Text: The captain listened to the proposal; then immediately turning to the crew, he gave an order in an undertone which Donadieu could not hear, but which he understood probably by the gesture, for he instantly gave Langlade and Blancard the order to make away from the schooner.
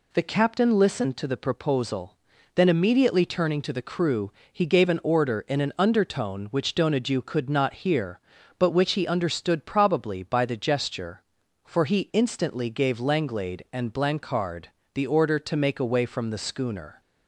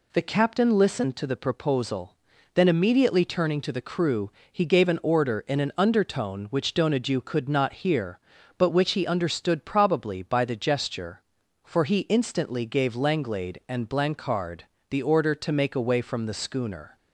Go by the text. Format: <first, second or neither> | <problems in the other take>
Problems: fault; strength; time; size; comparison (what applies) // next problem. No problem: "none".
neither | pauses between "Blancard" and "the"; slight; the same in both